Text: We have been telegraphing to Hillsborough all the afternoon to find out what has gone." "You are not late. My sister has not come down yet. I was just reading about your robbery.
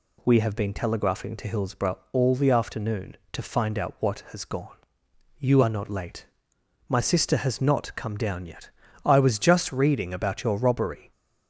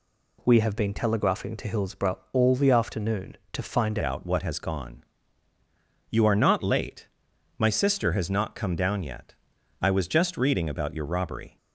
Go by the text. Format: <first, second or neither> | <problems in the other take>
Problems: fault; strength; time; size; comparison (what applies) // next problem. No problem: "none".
first | changes voice at "out"; from 4.0 s on; 7.5 s long